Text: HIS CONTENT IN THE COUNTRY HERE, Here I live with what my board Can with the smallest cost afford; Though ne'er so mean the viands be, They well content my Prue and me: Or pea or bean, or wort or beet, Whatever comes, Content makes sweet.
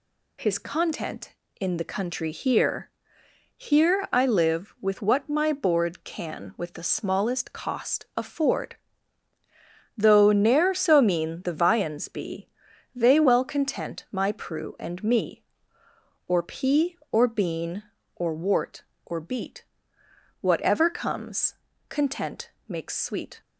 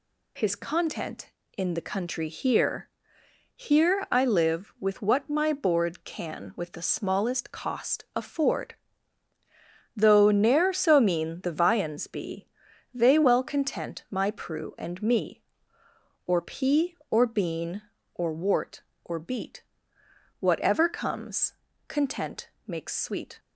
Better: neither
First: pauses between "Content" and "makes"; slight; at 22.5 s; 0.18 s long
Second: pauses between "Content" and "makes"; slight; at 22.4 s; 0.18 s long

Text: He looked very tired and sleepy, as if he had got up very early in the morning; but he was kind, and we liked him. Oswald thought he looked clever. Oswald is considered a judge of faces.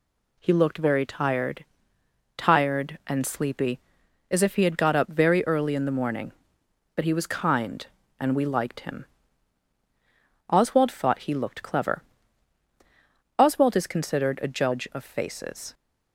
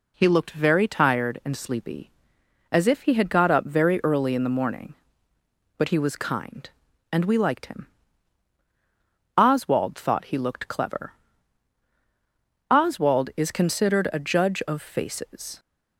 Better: second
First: says "tired" twice; at 2.3 s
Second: none

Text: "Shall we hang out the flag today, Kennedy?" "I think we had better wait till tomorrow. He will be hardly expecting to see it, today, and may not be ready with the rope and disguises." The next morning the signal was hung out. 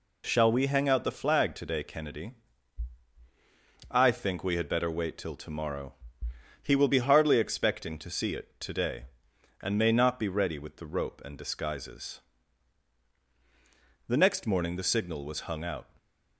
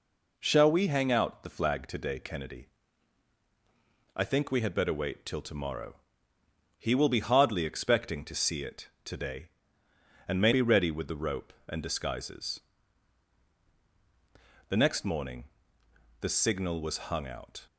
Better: first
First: none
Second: skips "not"; at 10.5 s // pauses between "morning" and "the"; noticeable; at 15.4 s; 0.78 s long

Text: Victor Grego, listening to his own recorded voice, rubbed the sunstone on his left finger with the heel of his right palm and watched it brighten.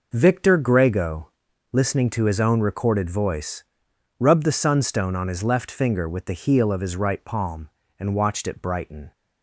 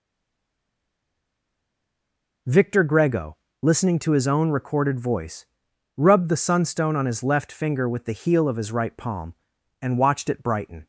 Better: first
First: none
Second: stays silent before the first word; until 2.4 s; 2.4 s long

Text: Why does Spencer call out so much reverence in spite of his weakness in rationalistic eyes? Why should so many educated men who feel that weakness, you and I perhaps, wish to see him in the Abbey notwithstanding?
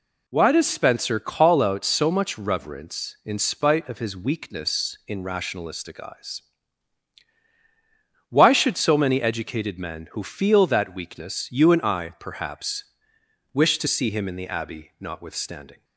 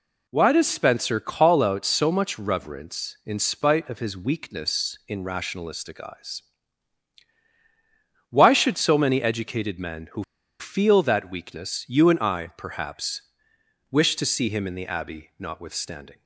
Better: first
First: none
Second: pauses between "who" and "feel"; at 10.2 s; 0.36 s long

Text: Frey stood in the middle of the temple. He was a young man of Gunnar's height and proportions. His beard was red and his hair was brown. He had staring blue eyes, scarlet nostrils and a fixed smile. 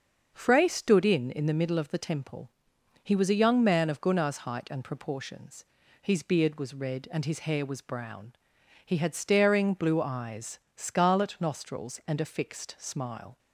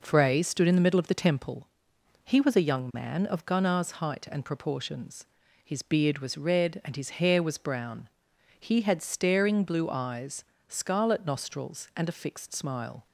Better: second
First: starts louder than the rest; until 1.3 s; 6.5 dB // says "in" twice; at 1.2 s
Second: none

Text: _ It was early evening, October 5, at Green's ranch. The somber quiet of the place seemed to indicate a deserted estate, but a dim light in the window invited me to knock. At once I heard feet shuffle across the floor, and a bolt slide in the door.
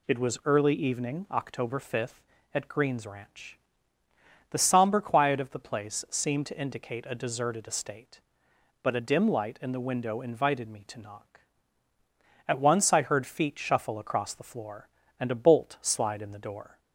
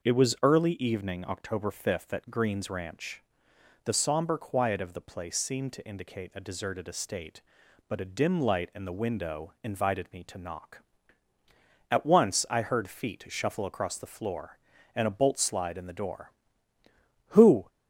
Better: first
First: none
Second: goes on to say "Who"; slight; from 17.2 s on; 0.40 s long

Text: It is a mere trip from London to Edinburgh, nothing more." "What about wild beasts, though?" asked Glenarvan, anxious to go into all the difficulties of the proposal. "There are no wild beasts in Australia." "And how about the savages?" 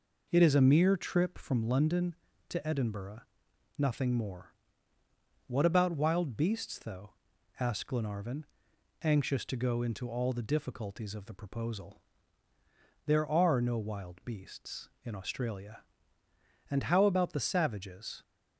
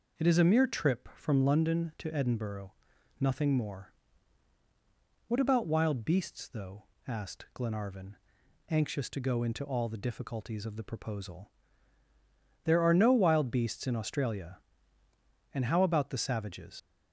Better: first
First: none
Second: leaves "savages" unfinished; at 16.7 s; 80 ms

